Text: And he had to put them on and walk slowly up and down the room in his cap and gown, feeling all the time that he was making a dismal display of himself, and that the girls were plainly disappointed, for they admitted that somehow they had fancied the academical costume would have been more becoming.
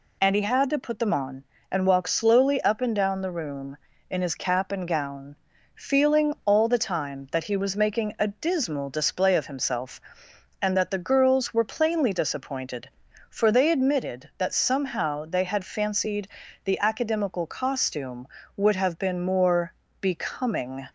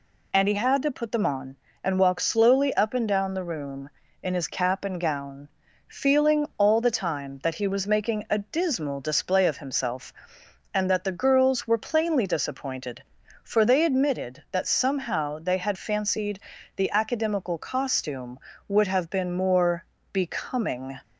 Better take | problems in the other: neither | pauses between "fancied" and "the"; slight; the same in both // pauses between "more" and "becoming"; slight; the same in both

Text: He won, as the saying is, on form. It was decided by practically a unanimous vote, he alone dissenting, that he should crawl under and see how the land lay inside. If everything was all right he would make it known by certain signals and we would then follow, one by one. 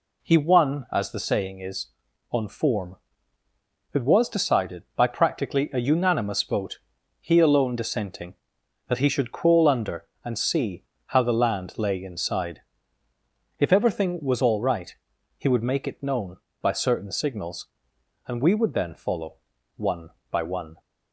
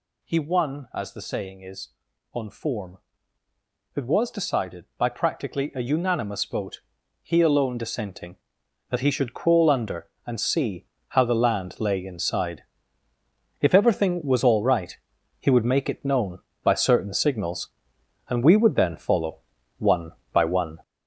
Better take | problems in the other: first | gets louder; throughout; 6.5 dB // pauses between "see" and "how"; slight; at 10.8 s; 0.22 s long; slight in the first // pauses between "right" and "he"; at 14.9 s; 0.42 s long; also in the first

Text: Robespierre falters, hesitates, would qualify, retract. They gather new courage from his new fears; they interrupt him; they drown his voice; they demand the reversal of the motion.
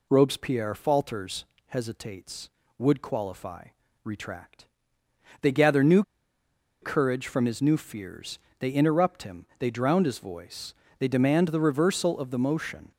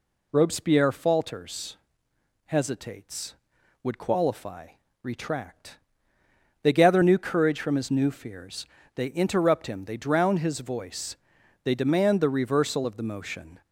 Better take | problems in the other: second | pauses between "new" and "courage"; noticeable; at 6.0 s; 0.80 s long

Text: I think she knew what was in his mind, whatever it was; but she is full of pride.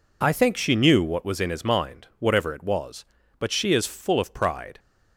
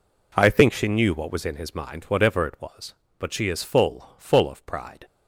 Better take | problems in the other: first | says "full" twice; at 4.1 s

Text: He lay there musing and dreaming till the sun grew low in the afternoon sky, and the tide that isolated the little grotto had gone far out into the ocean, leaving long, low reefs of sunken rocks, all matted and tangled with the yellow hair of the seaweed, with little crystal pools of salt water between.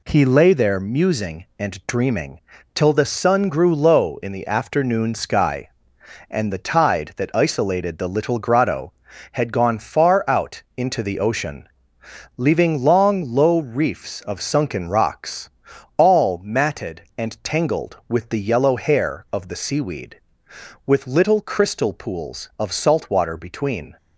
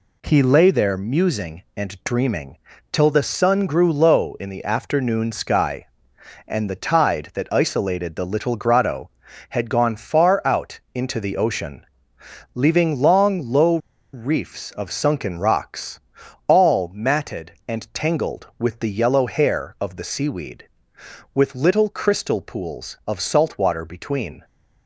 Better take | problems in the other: first | pauses between "dreaming" and "till"; slight; at 2.5 s; 0.34 s long; slight in the first // pauses between "low" and "reefs"; slight; at 13.7 s; 0.35 s long

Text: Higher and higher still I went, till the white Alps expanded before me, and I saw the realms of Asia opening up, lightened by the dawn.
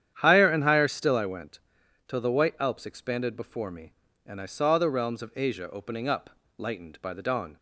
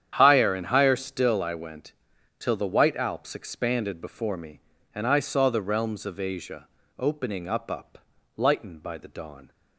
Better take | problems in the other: first | starts louder than the rest; strong; until 1.1 s; 9 dB; strong in the first // pauses between "Asia" and "opening"; slight; at 6.6 s; 0.32 s long // says "up" twice; at 7.7 s

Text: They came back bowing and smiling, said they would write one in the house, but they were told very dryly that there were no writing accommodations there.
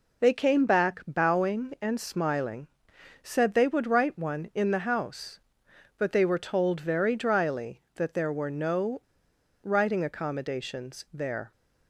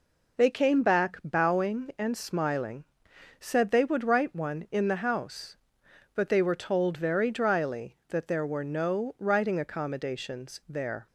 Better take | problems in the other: second | pauses between "no" and "writing"; noticeable; at 9.0 s; 0.62 s long

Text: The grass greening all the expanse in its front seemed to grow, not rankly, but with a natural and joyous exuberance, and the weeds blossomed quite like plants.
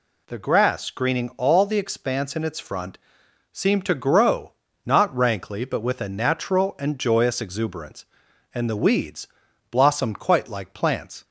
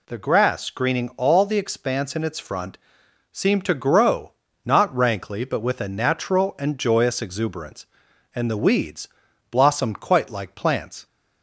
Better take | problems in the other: neither | pauses between "front" and "seemed"; noticeable; the same in both // pauses between "weeds" and "blossomed"; the same in both

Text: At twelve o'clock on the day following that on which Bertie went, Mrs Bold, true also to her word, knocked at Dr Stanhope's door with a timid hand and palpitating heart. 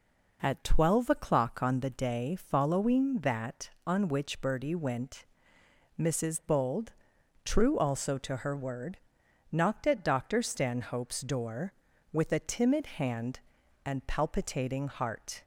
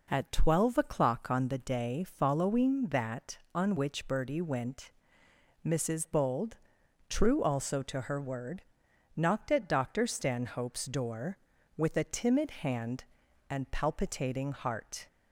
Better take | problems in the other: neither | none

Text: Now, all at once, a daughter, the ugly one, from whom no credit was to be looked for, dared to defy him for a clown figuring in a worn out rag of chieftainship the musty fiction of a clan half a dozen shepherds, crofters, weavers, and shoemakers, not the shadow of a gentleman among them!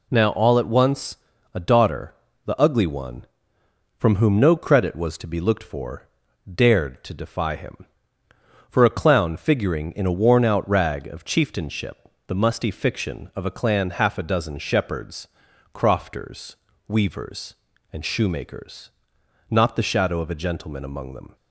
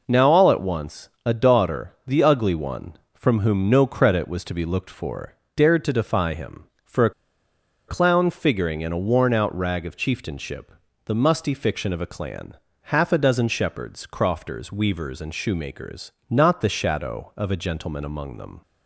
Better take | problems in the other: first | pauses between "a" and "clown"; noticeable; at 7.1 s; 0.77 s long // pauses between "chieftainship" and "the"; slight; at 10.7 s; 0.34 s long; slight in the first // pauses between "clan" and "half"; slight; at 12.5 s; 0.28 s long

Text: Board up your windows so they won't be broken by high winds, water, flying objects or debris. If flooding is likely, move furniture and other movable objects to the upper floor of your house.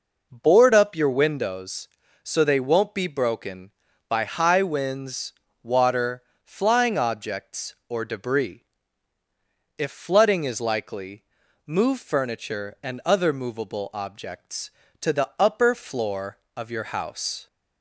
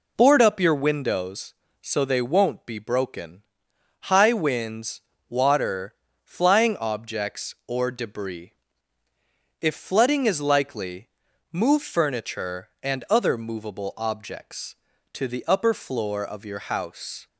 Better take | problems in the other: first | skips "by"; at 3.7 s

